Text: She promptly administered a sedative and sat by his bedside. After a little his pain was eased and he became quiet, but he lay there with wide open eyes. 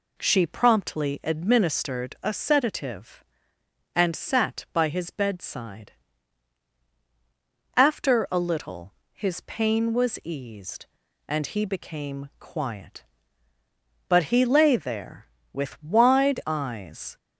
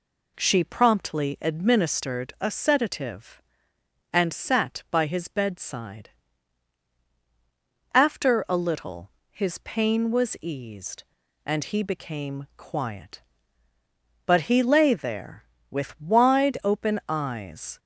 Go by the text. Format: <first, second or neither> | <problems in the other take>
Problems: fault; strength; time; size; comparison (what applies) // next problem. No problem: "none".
second | pauses between "little" and "his"; slight; at 8.9 s; 0.20 s long; slight in the second // skips "open"; at 16.4 s